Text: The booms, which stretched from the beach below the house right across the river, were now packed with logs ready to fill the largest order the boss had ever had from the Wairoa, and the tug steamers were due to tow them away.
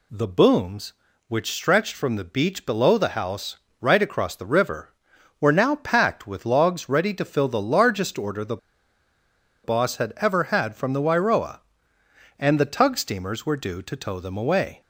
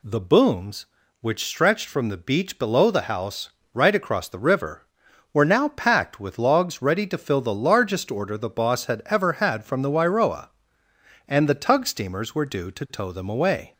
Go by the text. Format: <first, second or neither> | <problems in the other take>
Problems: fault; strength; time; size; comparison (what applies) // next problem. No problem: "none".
second | pauses between "house" and "right"; slight; at 3.5 s; 0.22 s long; slight in the second // pauses between "the" and "boss"; at 8.5 s; 1.0 s long